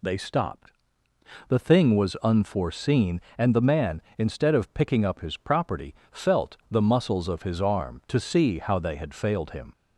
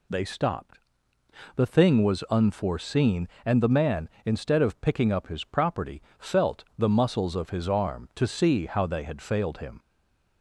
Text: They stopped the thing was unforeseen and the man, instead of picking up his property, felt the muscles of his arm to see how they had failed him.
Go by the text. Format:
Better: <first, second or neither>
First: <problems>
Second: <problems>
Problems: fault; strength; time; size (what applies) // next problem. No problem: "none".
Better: first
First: pauses between "stopped" and "the"; noticeable; at 0.7 s; 0.76 s long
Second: pauses between "stopped" and "the"; noticeable; at 0.7 s; 0.76 s long // stays silent after the last word; slight; from 9.7 s on; 0.7 s long